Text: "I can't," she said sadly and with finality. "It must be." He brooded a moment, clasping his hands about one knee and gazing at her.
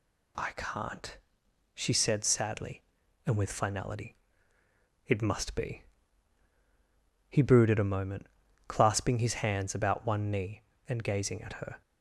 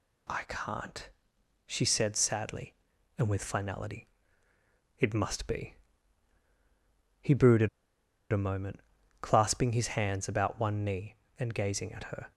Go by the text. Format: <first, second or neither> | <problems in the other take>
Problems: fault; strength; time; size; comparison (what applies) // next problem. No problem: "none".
first | pauses between "brooded" and "a"; noticeable; at 7.6 s; 0.64 s long